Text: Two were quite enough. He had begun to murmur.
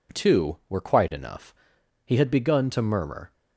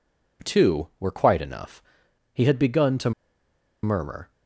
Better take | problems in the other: first | pauses between "to" and "murmur"; noticeable; at 3.1 s; 0.72 s long

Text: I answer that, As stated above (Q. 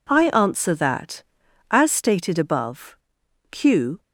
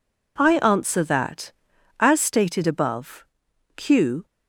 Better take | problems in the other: neither | none

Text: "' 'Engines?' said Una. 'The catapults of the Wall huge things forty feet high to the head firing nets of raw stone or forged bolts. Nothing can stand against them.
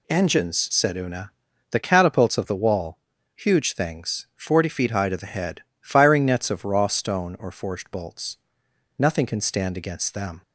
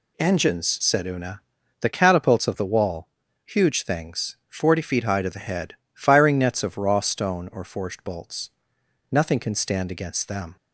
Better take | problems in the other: neither | pauses between "Wall" and "huge"; the same in both // pauses between "head" and "firing"; slight; the same in both

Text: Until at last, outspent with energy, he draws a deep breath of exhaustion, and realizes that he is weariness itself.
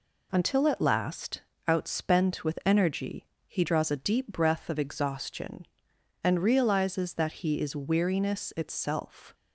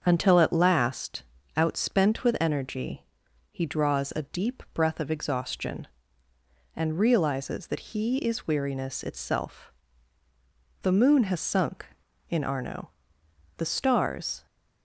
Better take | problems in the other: first | starts louder than the rest; until 1.0 s; 7 dB // goes on to say "The moon has sunk in Arno the stars"; strong; from 10.8 s on; 3.6 s long

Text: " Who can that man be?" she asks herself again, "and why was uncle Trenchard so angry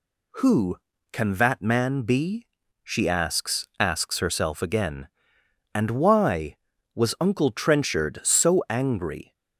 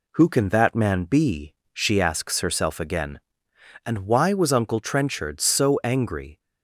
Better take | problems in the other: second | says "asks" twice; at 3.8 s

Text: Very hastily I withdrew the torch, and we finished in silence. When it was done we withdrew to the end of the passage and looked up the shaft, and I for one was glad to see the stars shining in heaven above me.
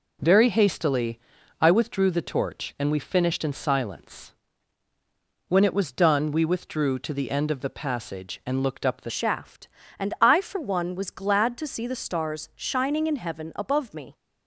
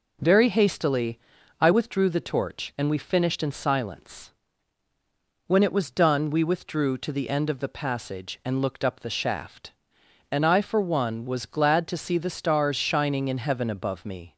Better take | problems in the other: second | pauses between "hastily" and "I"; at 1.1 s; 0.44 s long; also in the second // changes voice at "shaft"; from 9.0 s on; 5.1 s long

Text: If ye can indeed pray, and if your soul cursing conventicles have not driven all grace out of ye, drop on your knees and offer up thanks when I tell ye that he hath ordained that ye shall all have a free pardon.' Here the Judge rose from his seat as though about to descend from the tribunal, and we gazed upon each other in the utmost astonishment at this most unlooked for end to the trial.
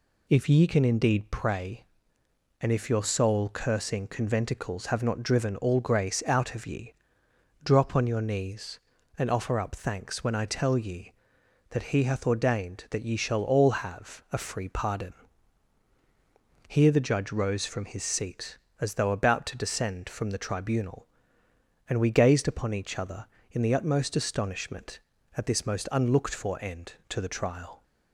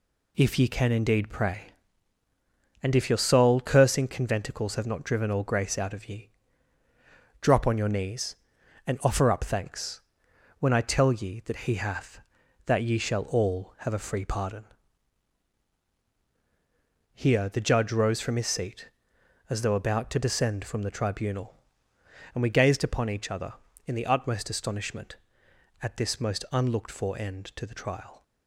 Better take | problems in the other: first | pauses between "thanks" and "when"; noticeable; at 10.0 s; 0.58 s long // skips "ordained"; at 12.4 s

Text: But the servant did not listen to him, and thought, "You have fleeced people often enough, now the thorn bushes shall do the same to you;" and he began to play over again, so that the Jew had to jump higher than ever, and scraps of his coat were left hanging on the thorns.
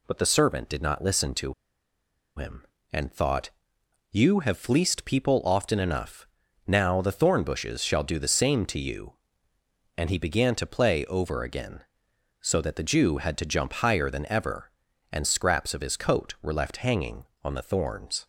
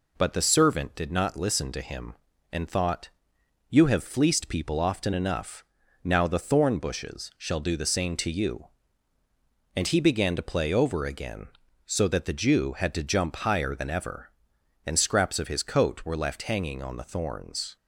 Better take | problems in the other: second | pauses between "to" and "him"; noticeable; at 1.5 s; 0.82 s long

